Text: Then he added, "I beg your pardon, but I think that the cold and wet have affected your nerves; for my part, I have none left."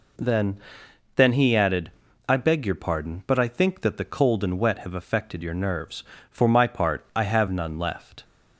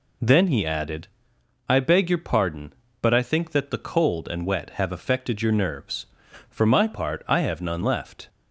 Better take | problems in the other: second | says "Then" twice; at 1.1 s

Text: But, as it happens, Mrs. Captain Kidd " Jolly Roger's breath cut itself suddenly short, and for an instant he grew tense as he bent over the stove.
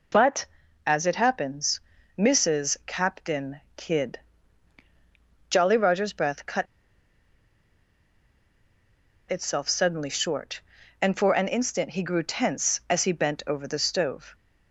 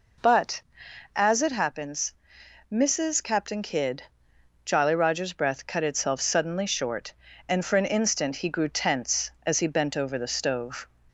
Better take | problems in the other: second | pauses between "Captain" and "Kidd"; slight; at 3.6 s; 0.16 s long // pauses between "cut" and "itself"; strong; at 6.6 s; 2.6 s long

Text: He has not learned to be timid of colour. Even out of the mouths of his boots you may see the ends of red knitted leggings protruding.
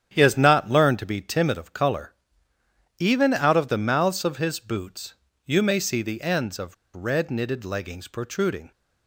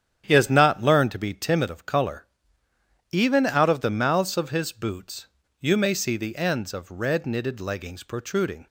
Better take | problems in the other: second | starts louder than the rest; strong; until 1.1 s; 9 dB; strong in the second // pauses between "boots" and "you"; slight; at 5.1 s; 0.32 s long; slight in the second // pauses between "of" and "red"; slight; at 6.7 s; 0.20 s long

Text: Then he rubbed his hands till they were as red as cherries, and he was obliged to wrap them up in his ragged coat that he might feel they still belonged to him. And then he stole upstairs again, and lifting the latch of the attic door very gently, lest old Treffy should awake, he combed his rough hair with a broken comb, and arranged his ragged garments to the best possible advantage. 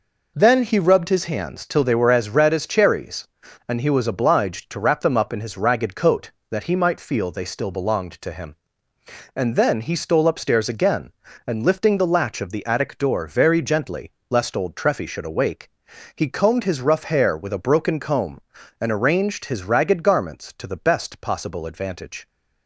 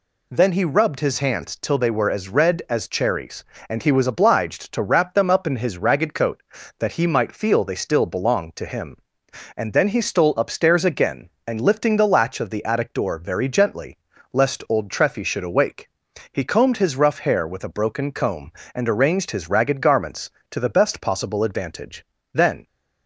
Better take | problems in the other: first | goes on to say "Then"; slight; from 22.3 s on; 0.32 s long

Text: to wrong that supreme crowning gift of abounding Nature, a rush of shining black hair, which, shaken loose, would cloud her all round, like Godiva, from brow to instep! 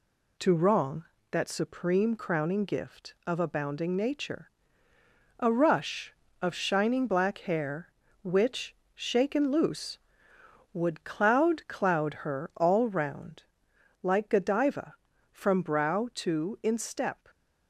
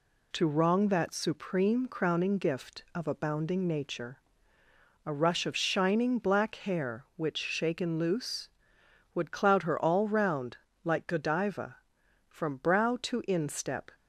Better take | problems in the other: second | says "cloud" twice; at 11.6 s

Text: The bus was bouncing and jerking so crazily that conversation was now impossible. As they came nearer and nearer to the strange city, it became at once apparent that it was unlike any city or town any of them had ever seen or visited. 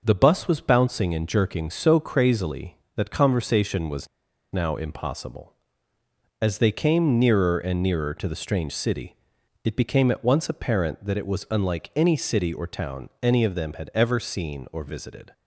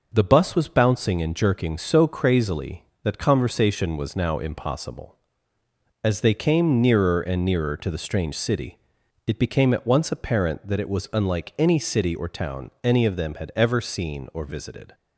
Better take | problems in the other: second | starts louder than the rest; noticeable; until 1.0 s; 6 dB; noticeable in the second // pauses between "was" and "now"; at 4.0 s; 0.45 s long

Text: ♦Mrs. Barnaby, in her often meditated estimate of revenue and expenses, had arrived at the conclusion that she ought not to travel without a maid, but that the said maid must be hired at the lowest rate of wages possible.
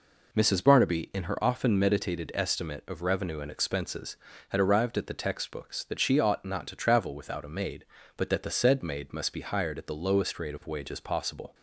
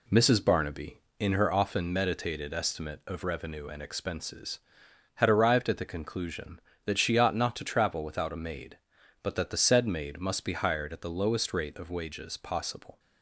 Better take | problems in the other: second | says "textbooks" for "conclusion"; at 5.1 s

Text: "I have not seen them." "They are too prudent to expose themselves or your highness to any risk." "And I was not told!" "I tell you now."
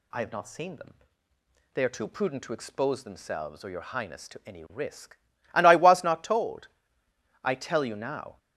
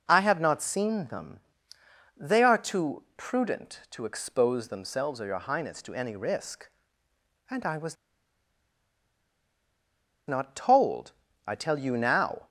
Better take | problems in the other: first | pauses between "was" and "not"; strong; at 7.9 s; 2.3 s long

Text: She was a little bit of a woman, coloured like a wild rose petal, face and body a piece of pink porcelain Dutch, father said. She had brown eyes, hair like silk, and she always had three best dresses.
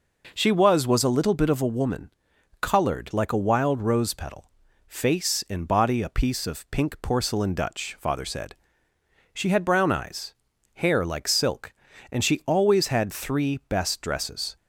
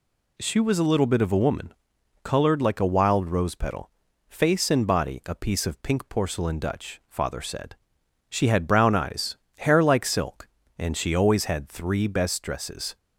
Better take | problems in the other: second | says "was" twice; at 0.8 s

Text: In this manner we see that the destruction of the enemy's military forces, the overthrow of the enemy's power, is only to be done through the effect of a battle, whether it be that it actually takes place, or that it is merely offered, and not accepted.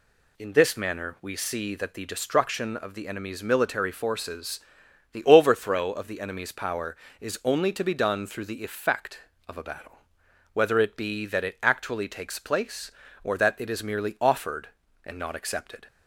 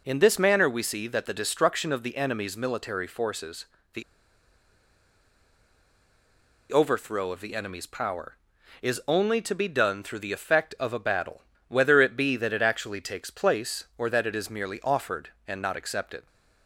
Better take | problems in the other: first | pauses between "the" and "overthrow"; strong; at 4.0 s; 2.6 s long

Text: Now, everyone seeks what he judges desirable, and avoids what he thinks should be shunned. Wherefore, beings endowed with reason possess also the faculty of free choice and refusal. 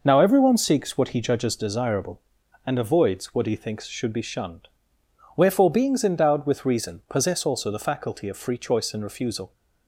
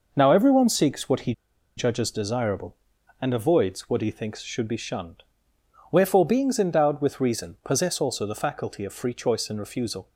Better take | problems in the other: first | pauses between "he" and "judges"; at 1.3 s; 0.45 s long

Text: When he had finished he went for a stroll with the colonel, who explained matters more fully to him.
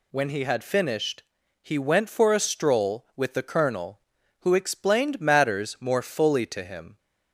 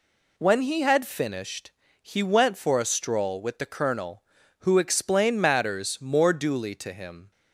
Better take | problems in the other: first | pauses between "finished" and "he"; slight; at 1.7 s; 0.32 s long; also in the first // says "duly" for "fully"; at 6.3 s

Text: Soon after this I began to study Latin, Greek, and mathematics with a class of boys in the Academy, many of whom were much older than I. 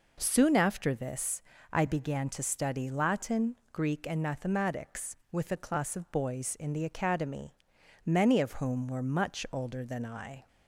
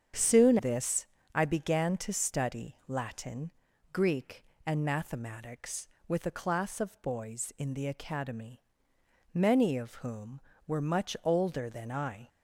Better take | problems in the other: first | starts louder than the rest; strong; until 1.5 s; 8 dB // skips "after"; at 0.5 s // pauses between "this" and "I"; slight; at 1.0 s; 0.30 s long; slight in the first

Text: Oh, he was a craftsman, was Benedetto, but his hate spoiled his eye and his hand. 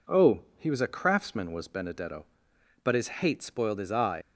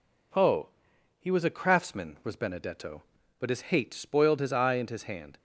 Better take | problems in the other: second | stops before "and his hand"; at 4.2 s

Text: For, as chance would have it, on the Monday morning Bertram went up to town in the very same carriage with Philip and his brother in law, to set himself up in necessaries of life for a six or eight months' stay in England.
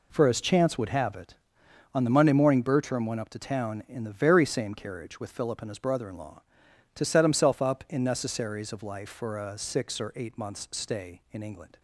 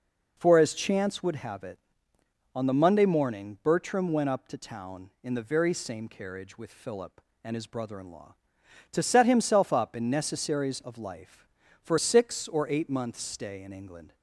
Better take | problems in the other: first | skips "a"; at 11.9 s

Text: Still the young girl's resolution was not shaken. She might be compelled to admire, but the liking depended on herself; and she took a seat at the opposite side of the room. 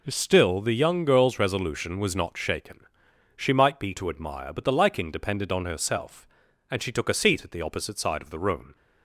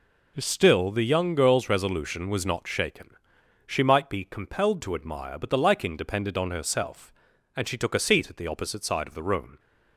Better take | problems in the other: second | skips "compelled"; at 3.9 s

